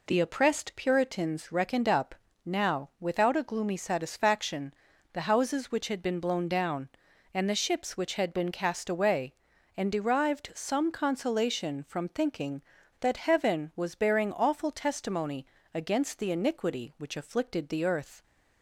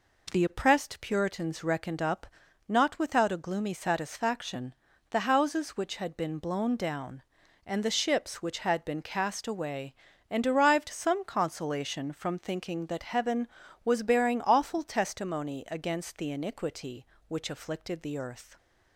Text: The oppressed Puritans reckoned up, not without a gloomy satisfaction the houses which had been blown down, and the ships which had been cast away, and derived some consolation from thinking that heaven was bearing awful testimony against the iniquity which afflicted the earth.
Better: second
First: says "now" for "not"; at 2.4 s // pauses between "satisfaction" and "the"; at 4.7 s; 0.42 s long // pauses between "testimony" and "against"; slight; at 15.4 s; 0.30 s long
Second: pauses between "satisfaction" and "the"; slight; at 4.7 s; 0.34 s long

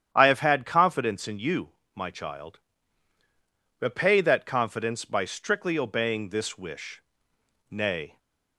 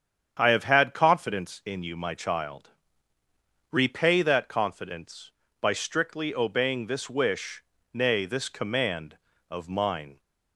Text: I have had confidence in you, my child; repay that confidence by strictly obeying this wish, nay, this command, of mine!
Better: second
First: starts louder than the rest; strong; until 1.1 s; 9.5 dB // stops before "this command of mine"; at 8.1 s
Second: starts louder than the rest; strong; until 1.4 s; 8.5 dB

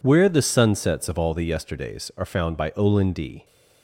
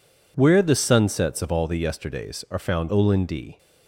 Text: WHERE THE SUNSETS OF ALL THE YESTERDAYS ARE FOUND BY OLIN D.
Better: first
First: none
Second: skips "BY"; at 2.8 s

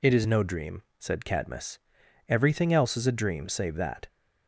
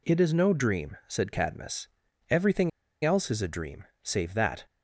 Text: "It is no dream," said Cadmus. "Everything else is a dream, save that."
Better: first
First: none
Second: pauses between "Everything" and "else"; slight; at 2.6 s; 0.35 s long

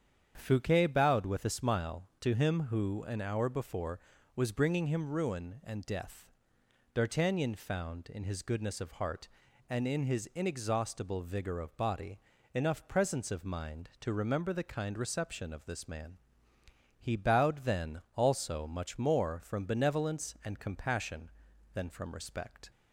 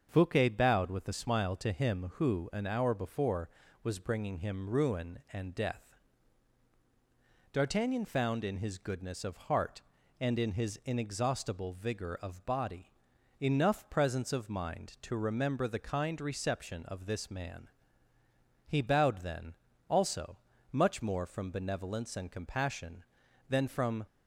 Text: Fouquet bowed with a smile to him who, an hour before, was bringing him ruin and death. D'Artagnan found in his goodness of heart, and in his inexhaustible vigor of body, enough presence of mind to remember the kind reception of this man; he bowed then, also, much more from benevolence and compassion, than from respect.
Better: first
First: starts louder than the rest; strong; until 1.3 s; 8 dB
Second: starts louder than the rest; until 1.1 s; 7 dB // stops before "respect"; at 24.0 s

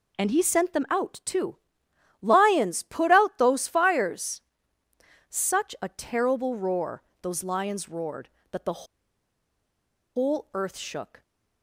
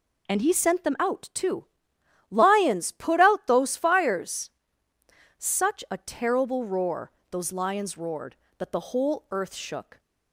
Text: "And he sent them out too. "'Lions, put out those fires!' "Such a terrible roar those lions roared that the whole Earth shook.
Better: second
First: pauses between "roar" and "those"; slight; at 7.0 s; 0.20 s long // pauses between "the" and "whole"; strong; at 8.8 s; 1.3 s long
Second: pauses between "roar" and "those"; slight; at 7.1 s; 0.20 s long

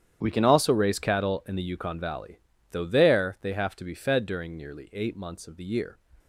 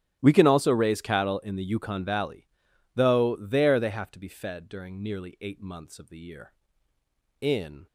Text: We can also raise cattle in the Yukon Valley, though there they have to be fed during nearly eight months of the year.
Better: first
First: starts louder than the rest; strong; until 1.2 s; 9.5 dB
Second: starts louder than the rest; strong; until 1.2 s; 11.5 dB // goes on to say "In"; slight; from 7.4 s on; 0.46 s long

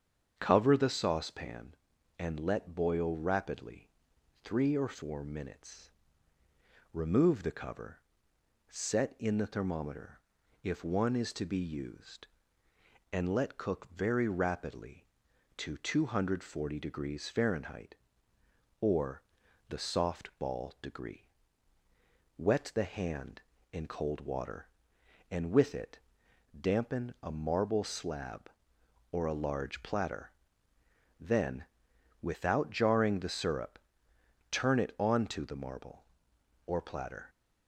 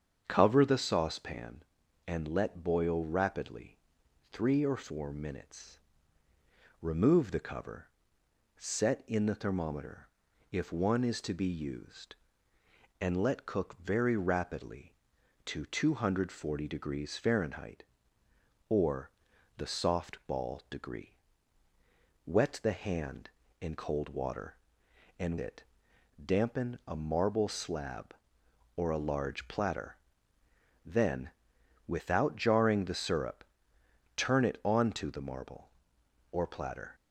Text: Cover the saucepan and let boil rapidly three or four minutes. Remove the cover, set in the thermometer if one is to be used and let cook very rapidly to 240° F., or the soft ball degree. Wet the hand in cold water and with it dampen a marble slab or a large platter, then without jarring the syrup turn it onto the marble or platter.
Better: first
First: starts louder than the rest; strong; until 1.3 s; 7.5 dB // pauses between "rapidly" and "three"; noticeable; at 3.8 s; 0.56 s long // pauses between "thermometer" and "if"; at 10.2 s; 0.42 s long // pauses between "or" and "the"; noticeable; at 19.2 s; 0.48 s long // pauses between "it" and "dampen"; noticeable; at 25.9 s; 0.60 s long // pauses between "then" and "without"; noticeable; at 31.6 s; 0.58 s long // pauses between "syrup" and "turn"; noticeable; at 33.7 s; 0.72 s long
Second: starts louder than the rest; strong; until 1.2 s; 7.5 dB // pauses between "rapidly" and "three"; noticeable; at 3.7 s; 0.56 s long // pauses between "thermometer" and "if"; at 10.0 s; 0.42 s long // pauses between "or" and "the"; noticeable; at 19.1 s; 0.48 s long // skips "with"; at 25.3 s // pauses between "it" and "dampen"; noticeable; at 25.6 s; 0.60 s long // pauses between "then" and "without"; noticeable; at 31.2 s; 0.58 s long // pauses between "syrup" and "turn"; noticeable; at 33.4 s; 0.72 s long

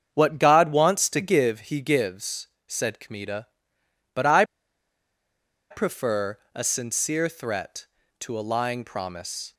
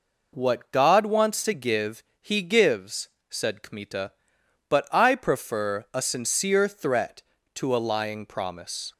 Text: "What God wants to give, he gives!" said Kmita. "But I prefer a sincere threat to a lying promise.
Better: second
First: starts louder than the rest; strong; until 1.1 s; 7.5 dB // pauses between "I" and "prefer"; strong; at 4.4 s; 1.2 s long // pauses between "prefer" and "a"; slight; at 6.3 s; 0.16 s long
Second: none

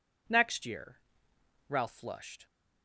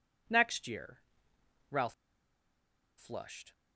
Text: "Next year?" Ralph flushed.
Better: first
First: none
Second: pauses between "Ralph" and "flushed"; at 1.9 s; 1.0 s long

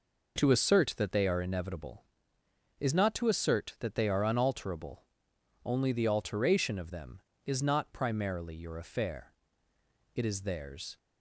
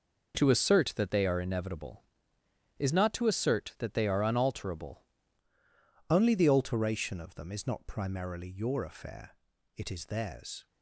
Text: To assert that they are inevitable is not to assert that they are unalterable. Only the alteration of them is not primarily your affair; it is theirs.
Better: first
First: none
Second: changes voice at "Only"; from 6.1 s on; 4.5 s long

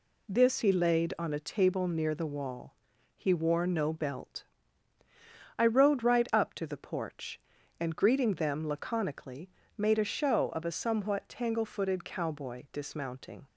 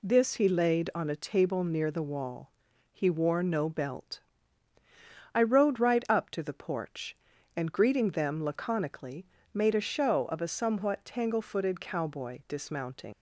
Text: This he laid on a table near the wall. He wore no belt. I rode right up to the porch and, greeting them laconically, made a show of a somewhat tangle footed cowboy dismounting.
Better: first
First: none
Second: leaves "dismounting" unfinished; at 13.1 s; 90 ms

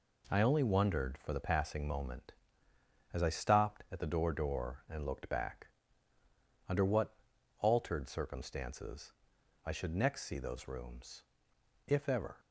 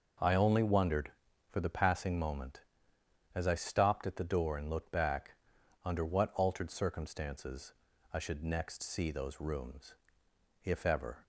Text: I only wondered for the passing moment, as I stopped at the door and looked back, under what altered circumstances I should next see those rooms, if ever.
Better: second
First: says "door" twice; at 4.3 s // pauses between "what" and "altered"; noticeable; at 7.1 s; 0.46 s long // pauses between "circumstances" and "I"; noticeable; at 9.1 s; 0.52 s long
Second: pauses between "circumstances" and "I"; at 7.7 s; 0.40 s long

